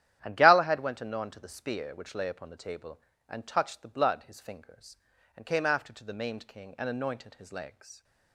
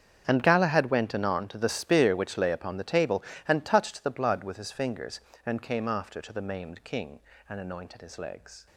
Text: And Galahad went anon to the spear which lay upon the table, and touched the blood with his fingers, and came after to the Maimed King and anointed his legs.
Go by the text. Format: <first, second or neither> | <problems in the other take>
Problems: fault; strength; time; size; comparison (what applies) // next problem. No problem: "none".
second | starts louder than the rest; strong; until 1.2 s; 11 dB; strong in the second // skips "with"; at 4.2 s